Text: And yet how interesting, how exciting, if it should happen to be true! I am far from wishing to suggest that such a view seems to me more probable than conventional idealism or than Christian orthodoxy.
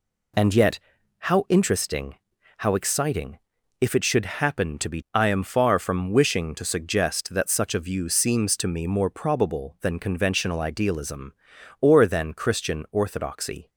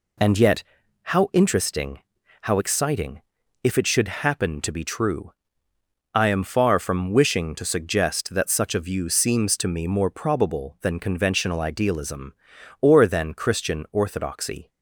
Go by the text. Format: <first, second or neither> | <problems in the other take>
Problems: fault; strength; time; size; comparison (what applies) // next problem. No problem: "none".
second | pauses between "yet" and "how"; at 0.7 s; 0.40 s long; also in the second // skips "true"; at 5.0 s